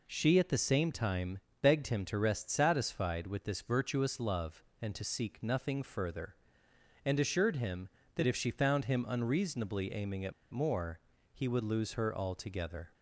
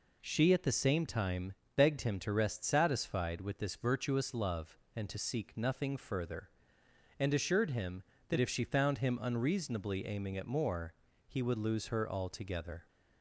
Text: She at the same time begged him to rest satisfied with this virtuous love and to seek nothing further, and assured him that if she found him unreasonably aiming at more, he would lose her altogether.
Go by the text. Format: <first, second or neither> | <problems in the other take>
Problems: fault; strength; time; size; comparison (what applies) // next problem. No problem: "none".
second | pauses between "time" and "begged"; slight; at 1.3 s; 0.22 s long; slight in the second // pauses between "at" and "more"; slight; at 10.3 s; 0.20 s long